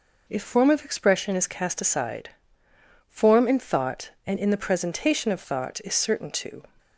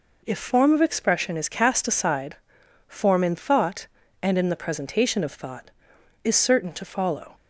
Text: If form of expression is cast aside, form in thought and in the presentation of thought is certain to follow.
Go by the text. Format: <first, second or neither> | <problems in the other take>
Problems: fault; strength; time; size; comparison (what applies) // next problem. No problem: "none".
second | stops before "follow"; at 6.7 s